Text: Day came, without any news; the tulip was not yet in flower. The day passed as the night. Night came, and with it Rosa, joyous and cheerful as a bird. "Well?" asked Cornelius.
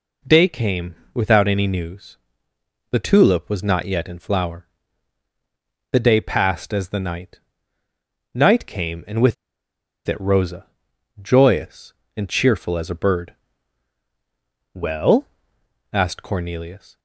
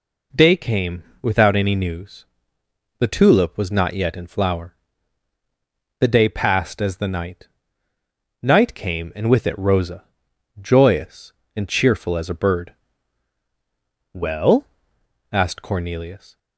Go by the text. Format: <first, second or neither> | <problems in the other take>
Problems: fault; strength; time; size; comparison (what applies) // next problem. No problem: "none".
second | pauses between "with" and "it"; noticeable; at 9.3 s; 0.71 s long